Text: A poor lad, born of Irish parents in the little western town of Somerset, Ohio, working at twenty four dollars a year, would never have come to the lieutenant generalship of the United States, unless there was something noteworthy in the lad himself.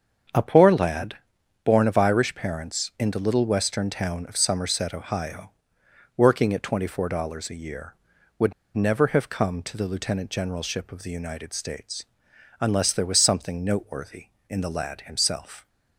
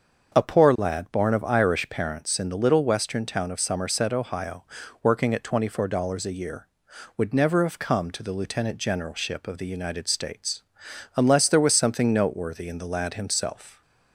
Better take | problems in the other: second | starts louder than the rest; strong; until 1.8 s; 7.5 dB; also in the second // pauses between "would" and "never"; slight; at 8.5 s; 0.22 s long

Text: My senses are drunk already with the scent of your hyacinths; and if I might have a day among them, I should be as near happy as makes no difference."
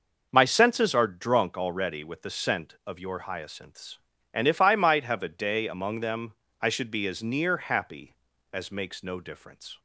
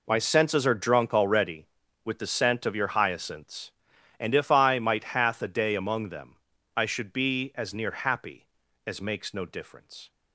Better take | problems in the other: first | says "hath" for "have"; at 5.0 s

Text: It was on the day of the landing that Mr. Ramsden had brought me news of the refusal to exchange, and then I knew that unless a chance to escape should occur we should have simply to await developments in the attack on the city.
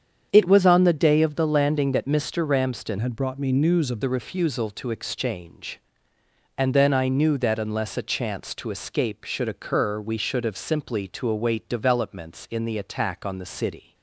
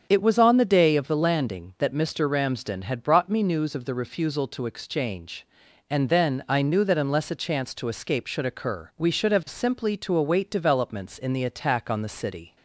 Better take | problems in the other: second | starts louder than the rest; strong; until 1.3 s; 8 dB; strong in the second // changes voice from "had" to "of"; from 2.9 to 4.0 s; 1.1 s long

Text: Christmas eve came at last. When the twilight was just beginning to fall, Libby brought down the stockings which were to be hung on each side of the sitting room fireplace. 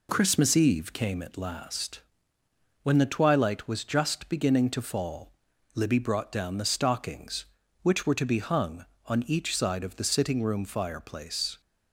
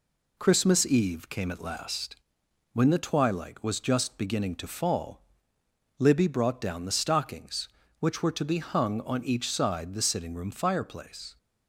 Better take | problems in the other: first | skips "of"; at 9.9 s

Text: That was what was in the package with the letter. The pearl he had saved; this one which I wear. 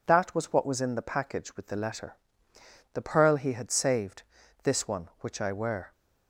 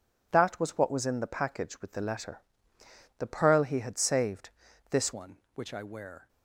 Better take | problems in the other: first | changes voice at "one"; from 5.1 s on; 1.1 s long

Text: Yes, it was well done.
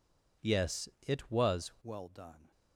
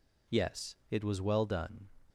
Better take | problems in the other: second | changes voice at "well"; from 1.8 s on; 0.7 s long

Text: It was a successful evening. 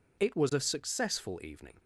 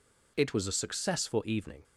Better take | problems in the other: neither | none

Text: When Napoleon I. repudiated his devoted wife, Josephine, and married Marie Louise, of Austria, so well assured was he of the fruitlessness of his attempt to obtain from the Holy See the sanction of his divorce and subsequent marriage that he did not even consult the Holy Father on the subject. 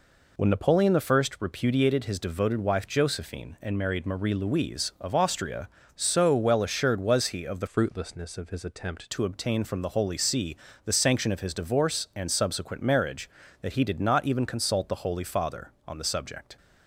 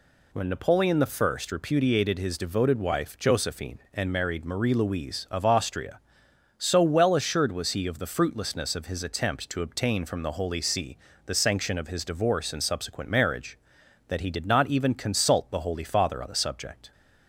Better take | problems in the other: second | pauses between "I" and "repudiated"; slight; at 1.2 s; 0.16 s long // changes voice from "fruitlessness" to "attempt"; from 7.6 to 9.0 s; 1.4 s long // pauses between "See" and "the"; slight; at 10.5 s; 0.28 s long; slight in the second

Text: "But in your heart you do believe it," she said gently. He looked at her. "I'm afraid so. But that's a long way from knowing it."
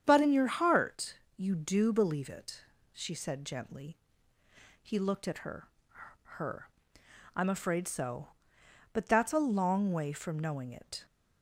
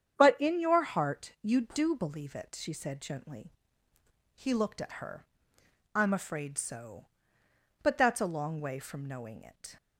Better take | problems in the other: second | starts louder than the rest; strong; until 1.0 s; 8 dB; strong in the second // pauses between "heart" and "you"; slight; at 1.1 s; 0.18 s long // says "her" twice; at 6.3 s

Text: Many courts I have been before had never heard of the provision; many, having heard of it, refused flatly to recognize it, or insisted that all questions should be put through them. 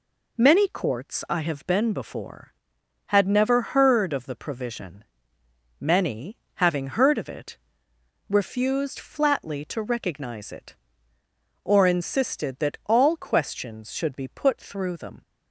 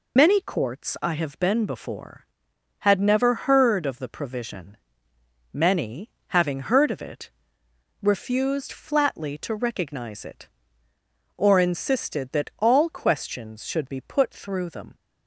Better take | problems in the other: first | loses the start of "Many"; at 0.1 s; 55 ms

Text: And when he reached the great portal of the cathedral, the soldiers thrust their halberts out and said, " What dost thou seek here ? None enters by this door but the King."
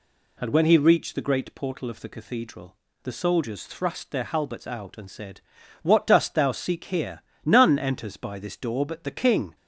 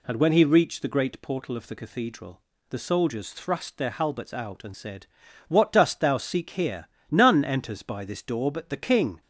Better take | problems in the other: neither | none

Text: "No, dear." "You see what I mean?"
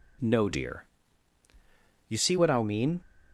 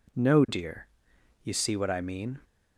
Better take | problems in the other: second | changes voice from "dear" to "see"; from 0.5 to 2.3 s; 1.8 s long

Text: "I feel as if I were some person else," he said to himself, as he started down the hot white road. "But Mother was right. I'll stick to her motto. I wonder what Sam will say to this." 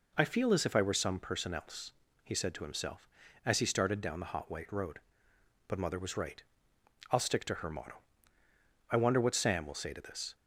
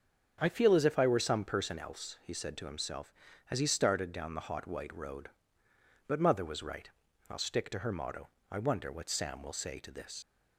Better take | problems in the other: first | starts louder than the rest; strong; until 1.4 s; 8 dB // leaves "this" unfinished; at 10.2 s; 70 ms

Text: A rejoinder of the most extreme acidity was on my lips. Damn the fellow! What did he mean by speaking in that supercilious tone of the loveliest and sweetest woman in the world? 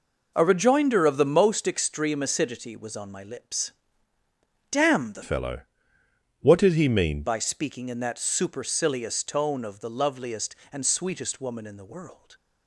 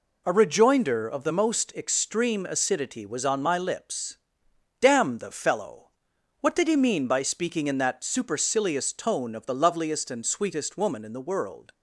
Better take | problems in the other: second | changes voice from "fellow" to "mean"; from 5.2 to 7.2 s; 2.0 s long

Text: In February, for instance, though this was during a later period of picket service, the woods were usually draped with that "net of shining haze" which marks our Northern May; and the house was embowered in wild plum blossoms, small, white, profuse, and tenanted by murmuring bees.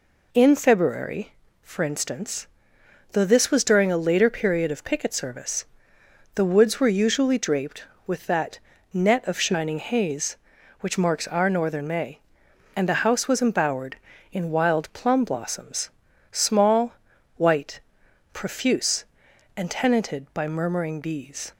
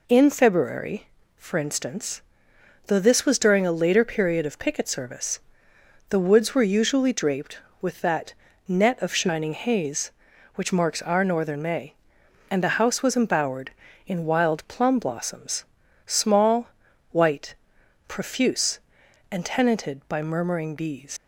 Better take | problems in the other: first | pauses between "that" and "net"; slight; at 8.3 s; 0.32 s long; slight in the first // leaves "bees" unfinished; at 21.1 s; 95 ms

